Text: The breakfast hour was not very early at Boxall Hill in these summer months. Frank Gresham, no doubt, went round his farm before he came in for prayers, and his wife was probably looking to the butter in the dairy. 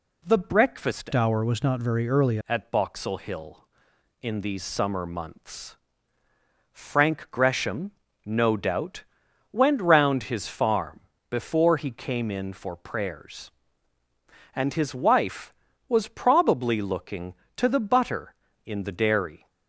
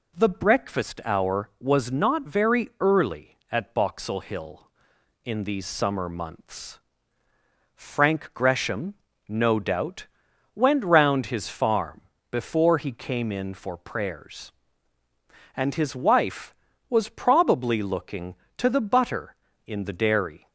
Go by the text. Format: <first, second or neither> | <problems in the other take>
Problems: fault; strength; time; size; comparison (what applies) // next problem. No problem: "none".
second | changes voice from "hour" to "early"; from 1.1 to 2.3 s; 1.2 s long // pauses between "farm" and "before"; slight; at 11.0 s; 0.30 s long; slight in the second